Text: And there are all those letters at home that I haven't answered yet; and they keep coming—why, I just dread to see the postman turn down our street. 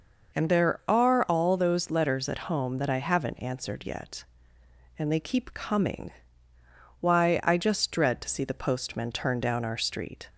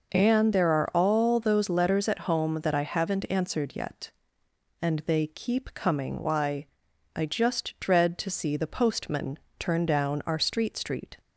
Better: first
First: none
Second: pauses between "postman" and "turn"; slight; at 9.3 s; 0.18 s long // says "street" twice; at 10.7 s

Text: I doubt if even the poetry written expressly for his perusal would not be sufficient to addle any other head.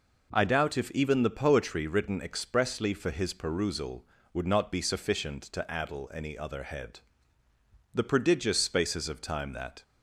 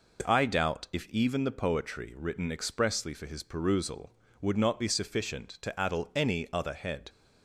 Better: second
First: goes on to say "The prodigious spaces of time that"; strong; from 7.9 s on; 1.9 s long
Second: none

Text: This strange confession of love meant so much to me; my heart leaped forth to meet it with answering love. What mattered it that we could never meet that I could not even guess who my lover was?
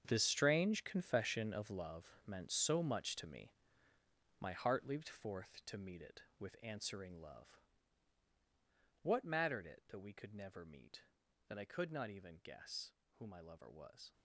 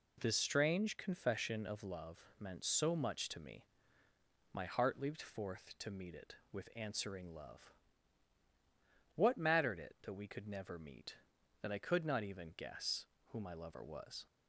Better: second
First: gets quieter; strong; throughout; 13.5 dB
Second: none

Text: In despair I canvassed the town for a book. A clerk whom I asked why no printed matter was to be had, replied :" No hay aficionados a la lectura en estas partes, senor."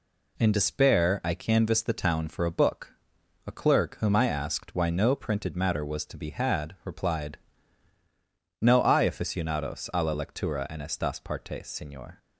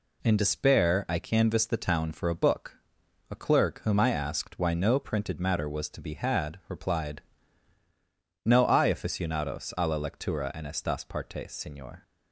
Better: neither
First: none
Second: none

